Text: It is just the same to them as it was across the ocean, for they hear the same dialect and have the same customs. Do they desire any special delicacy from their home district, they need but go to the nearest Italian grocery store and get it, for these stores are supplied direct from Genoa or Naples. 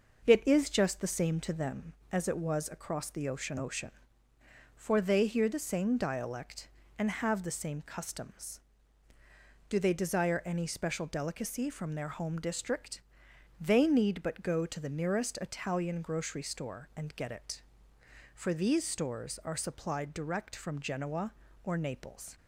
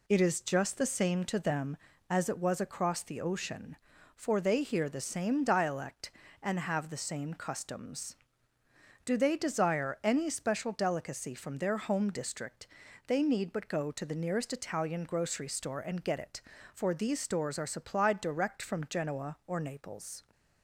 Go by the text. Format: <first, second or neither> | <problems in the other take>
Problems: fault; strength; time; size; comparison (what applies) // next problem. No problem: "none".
second | starts louder than the rest; noticeable; until 1.3 s; 6 dB // says "ocean" twice; at 3.5 s